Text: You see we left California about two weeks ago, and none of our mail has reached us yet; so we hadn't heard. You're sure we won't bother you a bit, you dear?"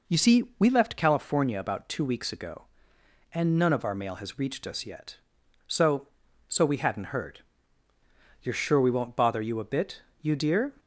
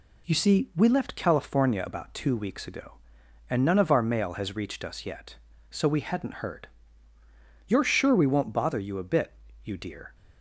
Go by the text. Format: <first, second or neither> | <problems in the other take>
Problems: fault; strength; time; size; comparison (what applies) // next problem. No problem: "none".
second | pauses between "see" and "we"; slight; at 0.4 s; 0.16 s long // says "so" twice; at 6.4 s